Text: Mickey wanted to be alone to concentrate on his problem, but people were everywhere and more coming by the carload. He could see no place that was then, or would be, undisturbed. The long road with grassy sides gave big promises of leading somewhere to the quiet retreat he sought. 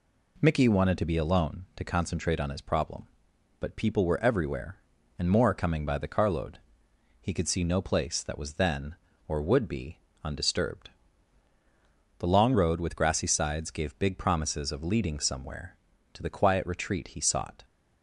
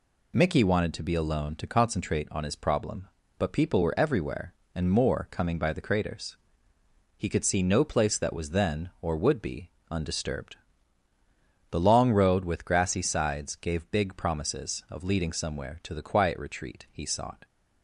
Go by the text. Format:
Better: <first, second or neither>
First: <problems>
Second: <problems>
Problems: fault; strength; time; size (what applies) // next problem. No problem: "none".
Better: first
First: none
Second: says "craters" for "carload"; at 5.8 s